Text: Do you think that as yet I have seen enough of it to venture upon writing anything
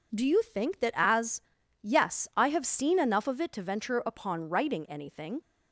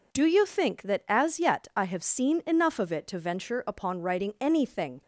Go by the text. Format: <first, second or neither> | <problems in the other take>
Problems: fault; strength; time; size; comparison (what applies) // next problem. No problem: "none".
second | says "yes" for "yet"; at 1.8 s